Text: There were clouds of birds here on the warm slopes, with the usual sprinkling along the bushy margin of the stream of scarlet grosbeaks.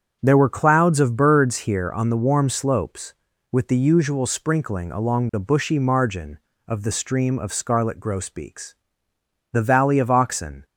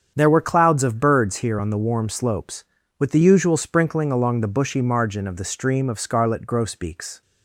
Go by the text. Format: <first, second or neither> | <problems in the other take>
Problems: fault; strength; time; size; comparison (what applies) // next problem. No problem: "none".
second | starts louder than the rest; strong; until 1.2 s; 7.5 dB; strong in the second // goes on to say "The valley of Oxen"; noticeable; from 9.5 s on; 1.1 s long